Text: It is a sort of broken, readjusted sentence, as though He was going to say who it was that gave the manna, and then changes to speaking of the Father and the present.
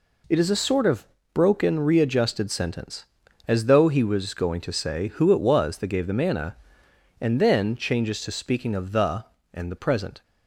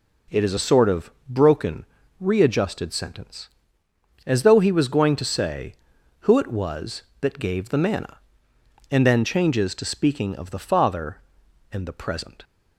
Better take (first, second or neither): second